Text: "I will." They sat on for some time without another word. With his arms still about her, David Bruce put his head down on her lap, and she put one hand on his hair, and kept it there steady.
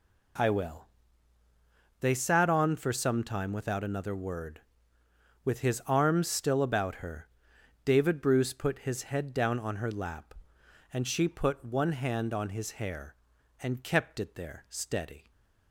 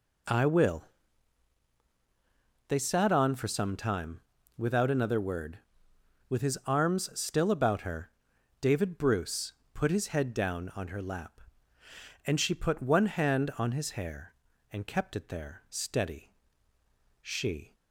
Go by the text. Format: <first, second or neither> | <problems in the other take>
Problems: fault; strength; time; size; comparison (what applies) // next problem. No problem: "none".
first | pauses between "time" and "without"; slight; at 4.2 s; 0.36 s long // pauses between "Bruce" and "put"; slight; at 9.5 s; 0.22 s long // goes on to say "She"; from 17.2 s on; 0.54 s long